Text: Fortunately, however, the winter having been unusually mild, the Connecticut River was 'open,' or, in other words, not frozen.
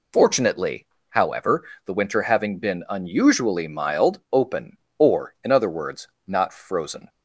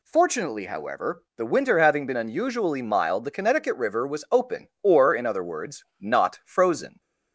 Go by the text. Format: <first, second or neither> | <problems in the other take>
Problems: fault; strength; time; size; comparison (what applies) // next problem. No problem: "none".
second | skips "the Connecticut River was"; at 4.2 s